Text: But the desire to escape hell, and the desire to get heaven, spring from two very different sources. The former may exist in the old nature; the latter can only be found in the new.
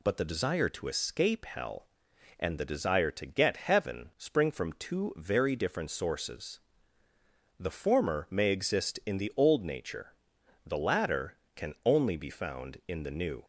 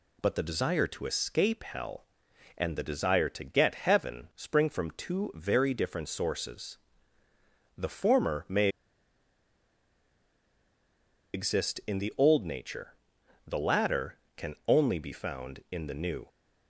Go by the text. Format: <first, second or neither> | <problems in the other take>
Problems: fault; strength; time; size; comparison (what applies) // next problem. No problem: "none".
first | pauses between "may" and "exist"; strong; at 8.6 s; 2.6 s long